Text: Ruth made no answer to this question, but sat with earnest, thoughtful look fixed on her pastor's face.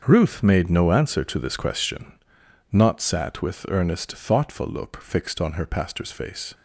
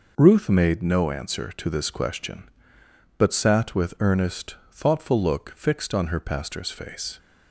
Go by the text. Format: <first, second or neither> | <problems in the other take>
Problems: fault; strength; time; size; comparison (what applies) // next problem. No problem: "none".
second | starts louder than the rest; until 1.0 s; 6.5 dB // says "not" for "but"; at 2.7 s